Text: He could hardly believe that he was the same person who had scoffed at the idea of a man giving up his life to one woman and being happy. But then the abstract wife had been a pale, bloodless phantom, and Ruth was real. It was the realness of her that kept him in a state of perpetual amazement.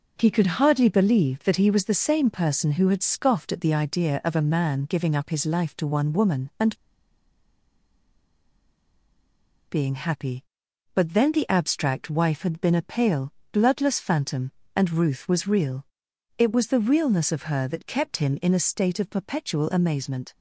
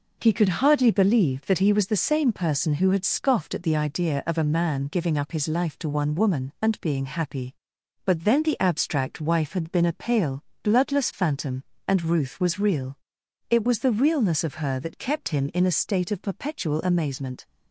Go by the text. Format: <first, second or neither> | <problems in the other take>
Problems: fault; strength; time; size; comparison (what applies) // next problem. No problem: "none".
second | pauses between "and" and "being"; strong; at 6.7 s; 2.9 s long